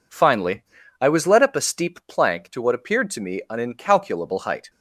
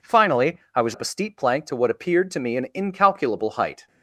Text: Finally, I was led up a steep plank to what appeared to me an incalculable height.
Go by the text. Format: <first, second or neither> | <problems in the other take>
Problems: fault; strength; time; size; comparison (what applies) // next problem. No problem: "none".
first | skips "led"; at 0.9 s